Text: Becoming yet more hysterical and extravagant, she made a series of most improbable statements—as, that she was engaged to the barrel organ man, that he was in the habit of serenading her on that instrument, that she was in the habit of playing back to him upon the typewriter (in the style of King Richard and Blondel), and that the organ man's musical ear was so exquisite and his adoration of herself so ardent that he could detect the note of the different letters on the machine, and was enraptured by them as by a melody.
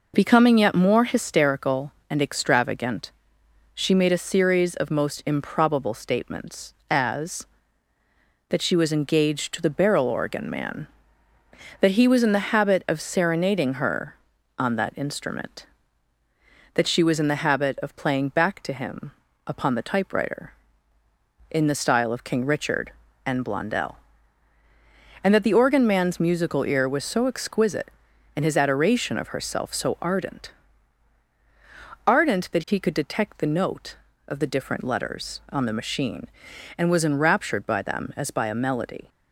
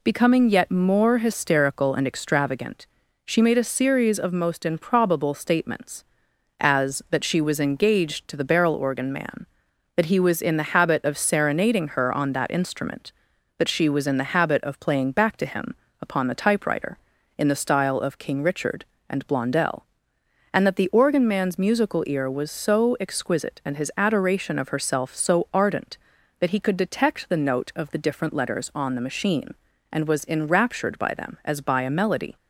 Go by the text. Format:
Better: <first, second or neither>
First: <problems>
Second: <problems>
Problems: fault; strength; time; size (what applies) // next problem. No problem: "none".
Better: second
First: pauses between "him" and "upon"; slight; at 19.1 s; 0.34 s long // says "ardent" twice; at 32.0 s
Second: pauses between "him" and "upon"; slight; at 15.7 s; 0.26 s long